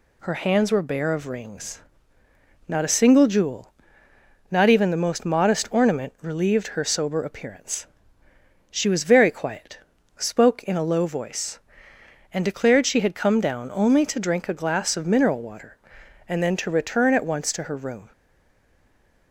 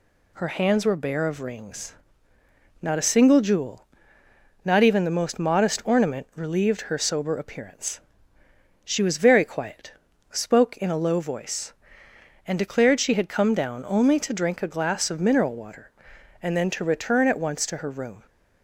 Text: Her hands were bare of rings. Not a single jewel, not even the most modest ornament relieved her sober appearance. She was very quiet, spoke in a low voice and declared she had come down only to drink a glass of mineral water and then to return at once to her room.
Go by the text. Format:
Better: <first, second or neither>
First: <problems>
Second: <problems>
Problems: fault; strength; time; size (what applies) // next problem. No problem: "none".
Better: second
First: stays silent after the last word; noticeable; from 18.1 s on; 1.2 s long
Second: none